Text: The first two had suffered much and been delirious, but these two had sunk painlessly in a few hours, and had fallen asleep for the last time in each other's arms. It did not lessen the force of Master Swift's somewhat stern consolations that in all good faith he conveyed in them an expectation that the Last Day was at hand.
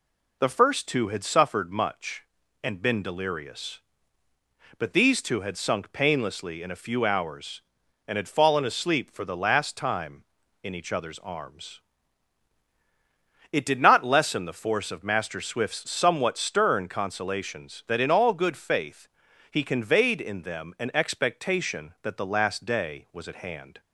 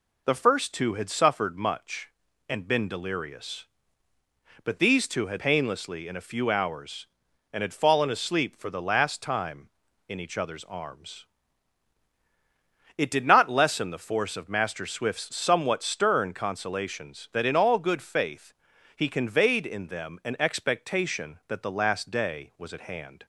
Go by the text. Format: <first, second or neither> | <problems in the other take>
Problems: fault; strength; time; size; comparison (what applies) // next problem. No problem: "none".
first | skips "sunk"; at 5.3 s // pauses between "faith" and "he"; at 18.5 s; 0.44 s long; also in the first